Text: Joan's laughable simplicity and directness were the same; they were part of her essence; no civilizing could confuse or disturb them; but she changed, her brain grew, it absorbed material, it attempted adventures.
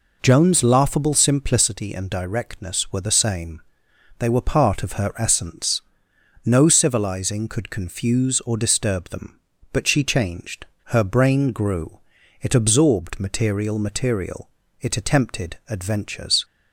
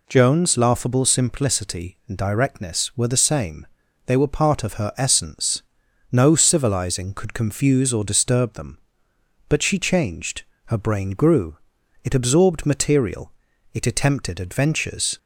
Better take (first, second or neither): second